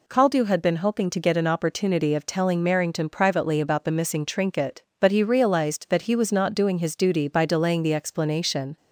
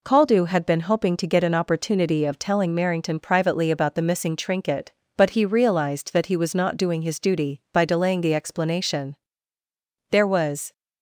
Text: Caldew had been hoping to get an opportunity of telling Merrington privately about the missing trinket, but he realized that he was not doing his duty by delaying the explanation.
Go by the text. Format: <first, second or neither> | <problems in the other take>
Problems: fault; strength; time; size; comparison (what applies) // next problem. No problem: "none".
first | goes on to say "There was"; noticeable; from 10.1 s on; 0.62 s long